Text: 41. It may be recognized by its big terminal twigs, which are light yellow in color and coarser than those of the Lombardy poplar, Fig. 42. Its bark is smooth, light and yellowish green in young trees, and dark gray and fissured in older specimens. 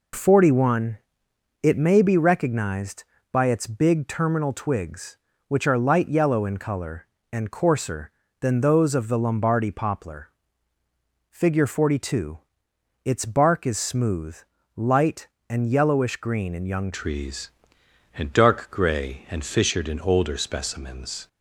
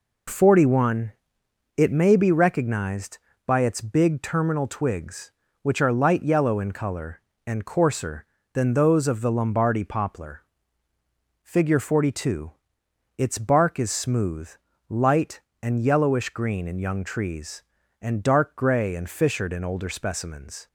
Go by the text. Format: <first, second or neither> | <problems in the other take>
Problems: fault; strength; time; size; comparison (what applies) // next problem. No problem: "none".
second | changes voice at "trees"; from 16.9 s on; 4.3 s long